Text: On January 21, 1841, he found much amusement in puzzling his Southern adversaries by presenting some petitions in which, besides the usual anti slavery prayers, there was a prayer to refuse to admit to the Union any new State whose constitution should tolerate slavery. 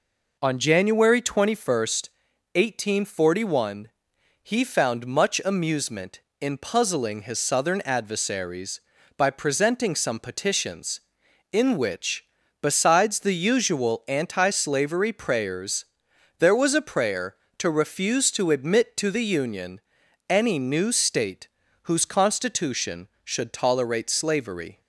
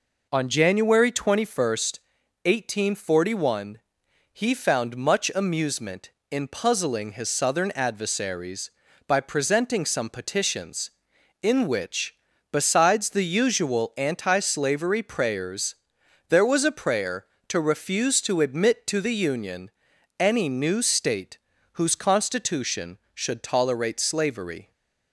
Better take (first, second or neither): neither